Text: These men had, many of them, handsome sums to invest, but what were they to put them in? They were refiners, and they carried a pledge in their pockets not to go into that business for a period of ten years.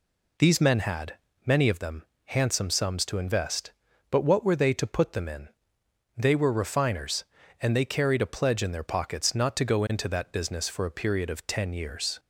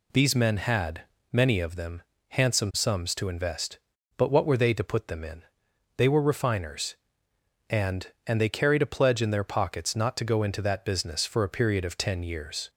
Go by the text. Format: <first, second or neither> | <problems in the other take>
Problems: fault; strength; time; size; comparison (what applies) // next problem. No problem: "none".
first | says "and" twice; at 8.2 s